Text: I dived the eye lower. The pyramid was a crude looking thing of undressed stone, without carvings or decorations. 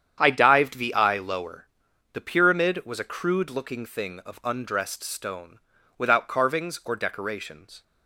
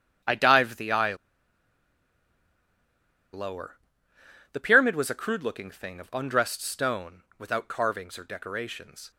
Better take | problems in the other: first | starts louder than the rest; strong; until 3.4 s; 8.5 dB; strong in the first // pauses between "eye" and "lower"; strong; at 1.1 s; 2.1 s long

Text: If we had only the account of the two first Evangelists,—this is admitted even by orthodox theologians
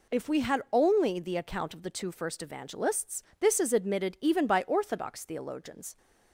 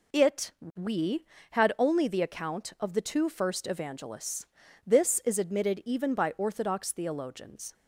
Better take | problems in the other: first | says "It" for "If"; at 0.1 s

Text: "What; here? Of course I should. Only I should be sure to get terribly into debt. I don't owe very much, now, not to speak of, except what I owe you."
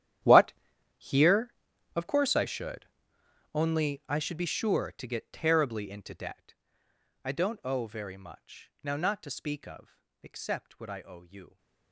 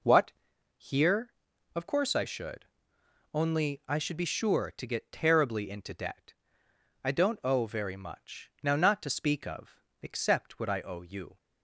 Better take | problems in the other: second | gets quieter; strong; throughout; 18 dB

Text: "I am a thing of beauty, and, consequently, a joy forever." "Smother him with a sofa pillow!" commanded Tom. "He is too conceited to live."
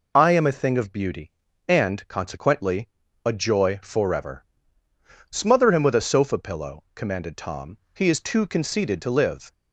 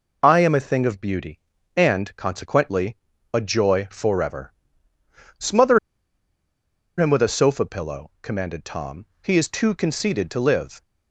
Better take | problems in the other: first | pauses between "Smother" and "him"; at 5.7 s; 1.1 s long

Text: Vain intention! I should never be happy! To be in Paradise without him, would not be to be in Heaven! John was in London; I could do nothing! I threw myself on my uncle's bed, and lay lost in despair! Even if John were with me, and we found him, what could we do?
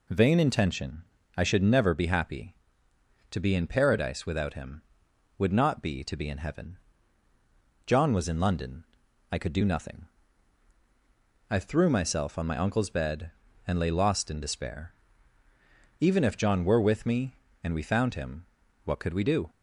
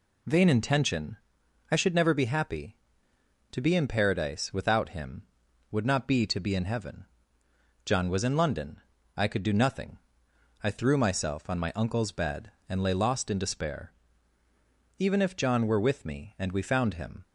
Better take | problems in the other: first | stops before "what could we do"; at 17.2 s

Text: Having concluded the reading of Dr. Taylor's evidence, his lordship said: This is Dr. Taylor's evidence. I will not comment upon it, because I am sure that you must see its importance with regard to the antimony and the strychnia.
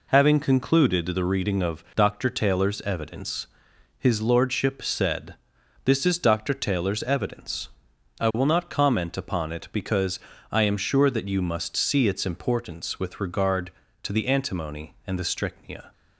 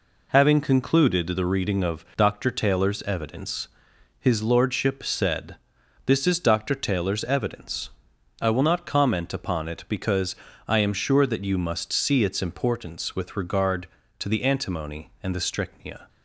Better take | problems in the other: neither | pauses between "because" and "I"; slight; the same in both

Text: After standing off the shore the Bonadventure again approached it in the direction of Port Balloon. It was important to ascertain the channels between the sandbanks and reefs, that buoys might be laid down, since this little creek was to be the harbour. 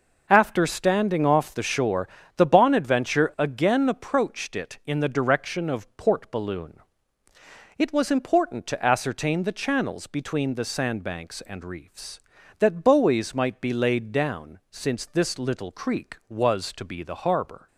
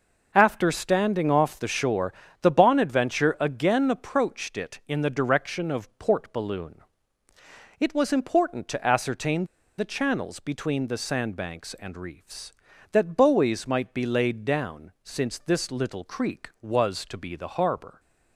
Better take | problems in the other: first | pauses between "shore" and "the"; slight; at 2.1 s; 0.30 s long; slight in the first // pauses between "ascertain" and "the"; slight; at 9.4 s; 0.33 s long

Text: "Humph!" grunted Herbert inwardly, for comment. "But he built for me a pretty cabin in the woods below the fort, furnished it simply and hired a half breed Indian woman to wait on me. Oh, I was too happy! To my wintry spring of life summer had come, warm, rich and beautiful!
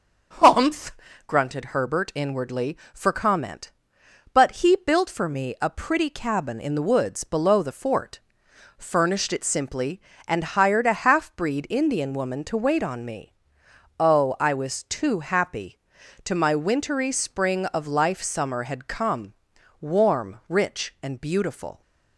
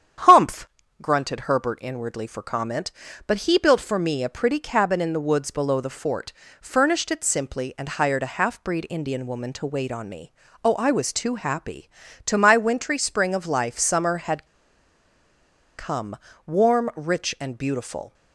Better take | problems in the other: first | starts louder than the rest; strong; until 1.6 s; 9 dB; also in the first // pauses between "had" and "come"; strong; at 14.4 s; 1.3 s long

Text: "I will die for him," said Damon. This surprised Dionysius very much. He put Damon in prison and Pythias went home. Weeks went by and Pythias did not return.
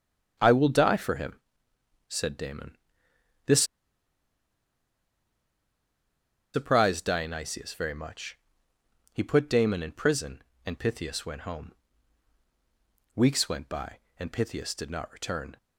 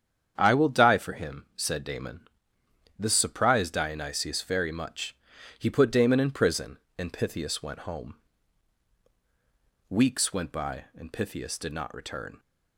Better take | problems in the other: second | starts louder than the rest; strong; until 1.4 s; 8 dB; strong in the second // pauses between "This" and "surprised"; strong; at 3.6 s; 2.9 s long

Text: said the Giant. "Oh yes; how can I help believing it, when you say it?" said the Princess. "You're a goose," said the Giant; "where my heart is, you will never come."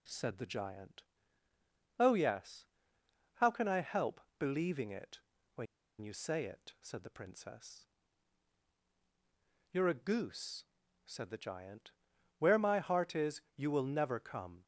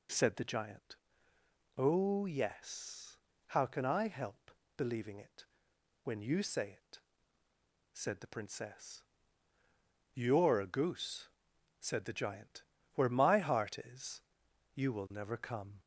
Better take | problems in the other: second | pauses between "help" and "believing"; slight; at 4.2 s; 0.18 s long; slight in the second // pauses between "when" and "you"; slight; at 5.6 s; 0.35 s long

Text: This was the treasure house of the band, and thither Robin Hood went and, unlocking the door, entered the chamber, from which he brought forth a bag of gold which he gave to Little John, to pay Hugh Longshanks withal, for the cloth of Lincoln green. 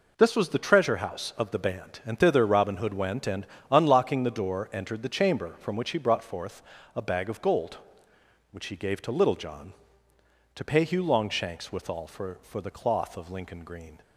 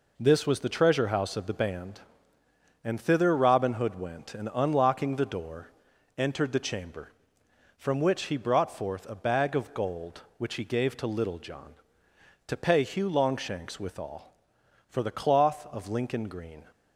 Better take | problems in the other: second | pauses between "forth" and "a"; slight; at 6.6 s; 0.32 s long // says "for" twice; at 12.4 s

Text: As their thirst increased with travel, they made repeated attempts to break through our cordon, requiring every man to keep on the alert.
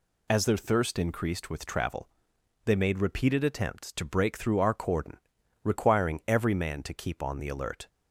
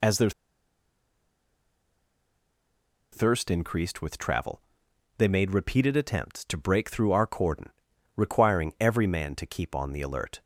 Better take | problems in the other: first | pauses between "their" and "thirst"; strong; at 0.3 s; 2.8 s long

